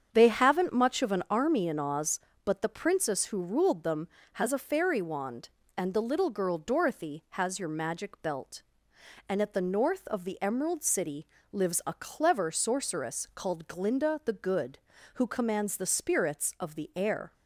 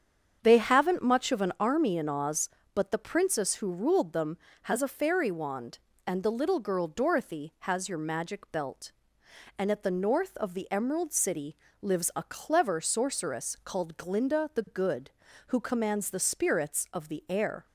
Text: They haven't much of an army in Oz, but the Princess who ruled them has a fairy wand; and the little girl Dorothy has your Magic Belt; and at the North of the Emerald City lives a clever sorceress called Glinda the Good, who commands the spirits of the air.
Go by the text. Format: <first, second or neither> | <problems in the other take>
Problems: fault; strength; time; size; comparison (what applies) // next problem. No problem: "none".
neither | starts louder than the rest; strong; the same in both // pauses between "City" and "lives"; slight; the same in both